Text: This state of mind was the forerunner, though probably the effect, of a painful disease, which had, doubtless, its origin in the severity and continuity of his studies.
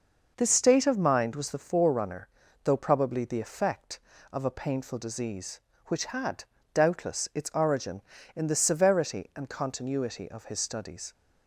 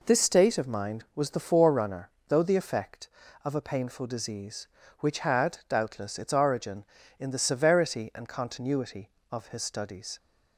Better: first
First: none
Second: skips "probably"; at 2.4 s

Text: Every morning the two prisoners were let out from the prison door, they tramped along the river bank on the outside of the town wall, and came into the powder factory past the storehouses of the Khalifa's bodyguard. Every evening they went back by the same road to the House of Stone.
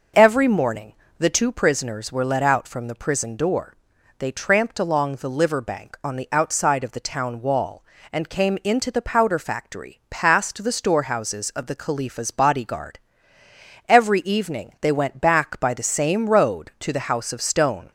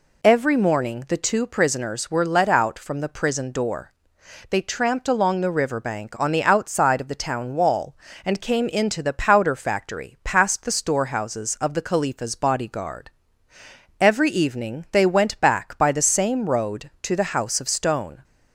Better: second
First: pauses between "morning" and "the"; slight; at 0.9 s; 0.24 s long // says "liver" for "river"; at 5.3 s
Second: none

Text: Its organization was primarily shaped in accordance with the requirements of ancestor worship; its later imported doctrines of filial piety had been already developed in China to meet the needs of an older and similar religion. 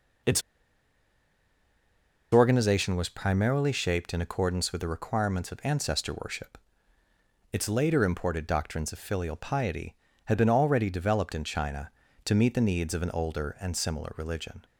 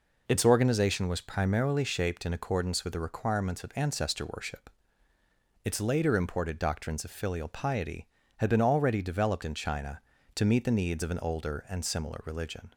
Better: second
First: pauses between "Its" and "organization"; strong; at 0.4 s; 1.9 s long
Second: none

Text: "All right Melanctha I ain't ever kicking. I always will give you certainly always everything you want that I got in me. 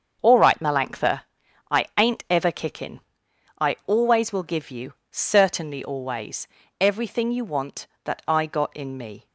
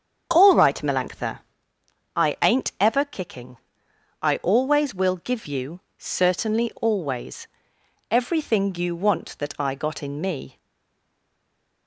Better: first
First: starts louder than the rest; until 1.2 s; 7 dB // pauses between "Melanctha" and "I"; noticeable; at 1.2 s; 0.50 s long // pauses between "you" and "certainly"; slight; at 4.9 s; 0.18 s long // pauses between "always" and "everything"; slight; at 6.4 s; 0.36 s long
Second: starts louder than the rest; strong; until 1.3 s; 7.5 dB // pauses between "Melanctha" and "I"; noticeable; at 1.3 s; 0.76 s long // pauses between "you" and "certainly"; slight; at 5.7 s; 0.18 s long // pauses between "always" and "everything"; noticeable; at 7.4 s; 0.62 s long // stays silent after the last word; noticeable; from 10.5 s on; 1.3 s long

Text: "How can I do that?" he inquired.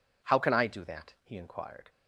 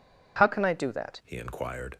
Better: first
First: none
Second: changes voice at "he"; from 1.2 s on; 0.7 s long

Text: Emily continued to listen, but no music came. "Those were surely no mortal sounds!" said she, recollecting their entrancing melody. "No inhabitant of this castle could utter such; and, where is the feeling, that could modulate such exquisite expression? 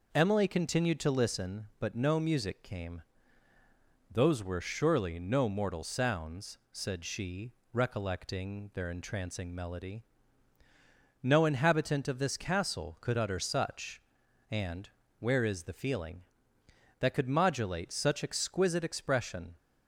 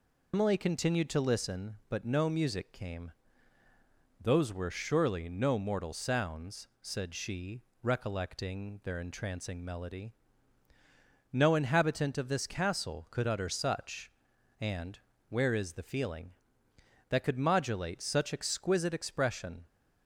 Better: first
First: none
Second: loses the start of "Emily"; at 0.3 s; 115 ms

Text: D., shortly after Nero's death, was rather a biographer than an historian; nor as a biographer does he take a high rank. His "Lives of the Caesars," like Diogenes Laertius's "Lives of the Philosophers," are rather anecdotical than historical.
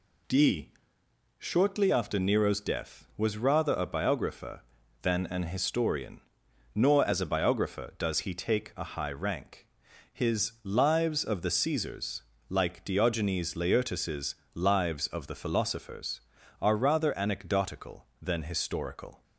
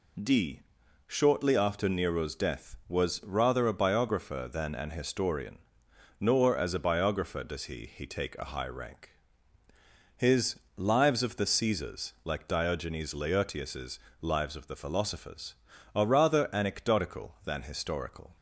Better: first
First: pauses between "Laertius's" and "Lives"; slight; at 14.3 s; 0.18 s long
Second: says "he" twice; at 7.8 s // pauses between "His" and "Lives"; slight; at 10.5 s; 0.16 s long // pauses between "Laertius's" and "Lives"; slight; at 13.9 s; 0.20 s long

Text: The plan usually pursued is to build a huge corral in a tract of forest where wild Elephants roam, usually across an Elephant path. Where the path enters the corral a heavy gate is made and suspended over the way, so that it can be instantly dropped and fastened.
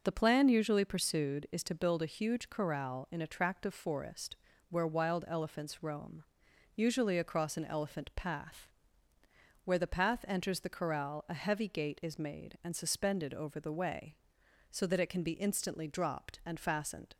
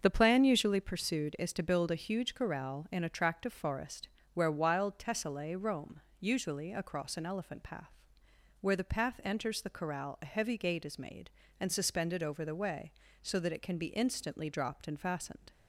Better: first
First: pauses between "forest" and "where"; slight; at 4.3 s; 0.32 s long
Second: starts louder than the rest; until 1.0 s; 6.5 dB // pauses between "forest" and "where"; slight; at 4.0 s; 0.24 s long // says "Tessellae" for "Elephants"; at 4.9 s

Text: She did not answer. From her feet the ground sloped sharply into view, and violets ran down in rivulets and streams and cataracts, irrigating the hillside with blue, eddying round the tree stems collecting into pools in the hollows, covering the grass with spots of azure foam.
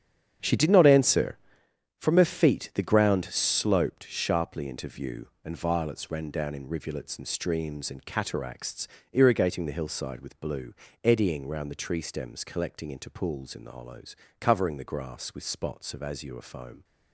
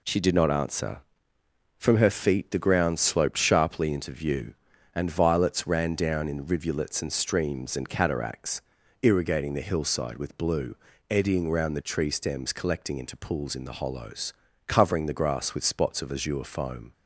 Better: second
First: starts louder than the rest; strong; until 1.7 s; 8.5 dB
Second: none

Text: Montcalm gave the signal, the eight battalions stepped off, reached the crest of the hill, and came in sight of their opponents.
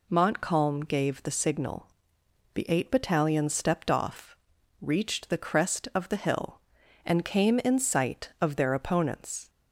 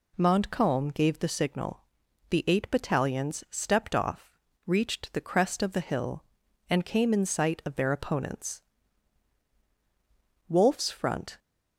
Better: first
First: none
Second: goes on to say "Wolfe's front"; noticeable; from 10.4 s on; 0.90 s long

